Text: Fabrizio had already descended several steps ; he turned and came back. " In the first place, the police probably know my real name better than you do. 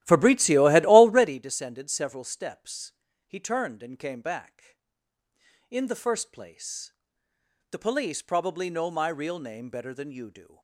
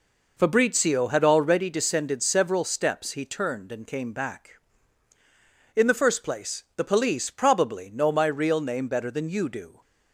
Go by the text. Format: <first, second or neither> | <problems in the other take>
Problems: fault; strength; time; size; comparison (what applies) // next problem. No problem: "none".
second | starts louder than the rest; strong; until 1.4 s; 14.5 dB